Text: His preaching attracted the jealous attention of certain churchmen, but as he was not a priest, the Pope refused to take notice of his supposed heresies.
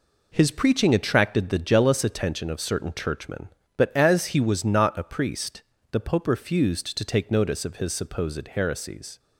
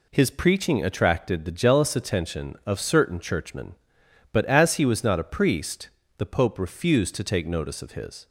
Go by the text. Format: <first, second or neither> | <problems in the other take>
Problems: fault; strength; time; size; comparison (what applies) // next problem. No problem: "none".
first | stops before "supposed heresies"; at 8.2 s